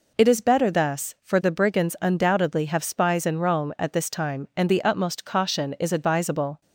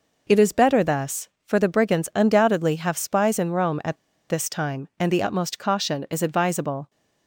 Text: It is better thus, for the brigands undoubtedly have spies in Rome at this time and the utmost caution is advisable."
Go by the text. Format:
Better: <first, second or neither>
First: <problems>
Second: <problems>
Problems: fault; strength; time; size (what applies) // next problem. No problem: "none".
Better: first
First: none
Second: pauses between "at" and "this"; slight; at 3.9 s; 0.32 s long